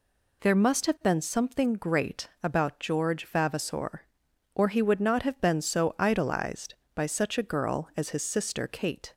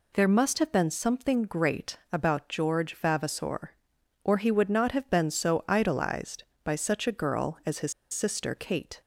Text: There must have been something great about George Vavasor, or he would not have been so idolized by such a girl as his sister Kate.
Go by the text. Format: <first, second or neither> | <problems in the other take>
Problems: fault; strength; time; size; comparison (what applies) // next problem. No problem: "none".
first | pauses between "his" and "sister"; slight; at 7.9 s; 0.18 s long